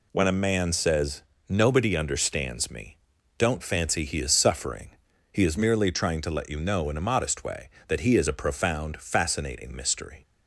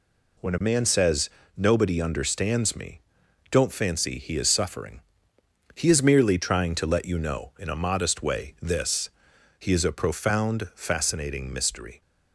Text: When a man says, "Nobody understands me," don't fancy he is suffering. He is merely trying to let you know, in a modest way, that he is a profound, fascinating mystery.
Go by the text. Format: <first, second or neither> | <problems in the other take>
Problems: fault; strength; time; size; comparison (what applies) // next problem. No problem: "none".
first | says "this" for "that"; at 8.6 s